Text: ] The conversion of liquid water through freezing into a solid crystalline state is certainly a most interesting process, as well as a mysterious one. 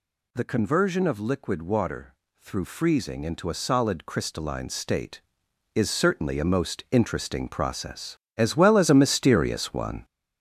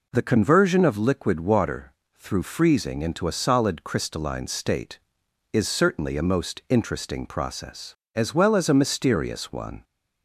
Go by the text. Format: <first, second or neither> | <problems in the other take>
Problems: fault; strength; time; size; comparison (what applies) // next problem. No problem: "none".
second | gets louder; throughout; 7 dB // pauses between "water" and "through"; slight; at 2.1 s; 0.26 s long; slight in the second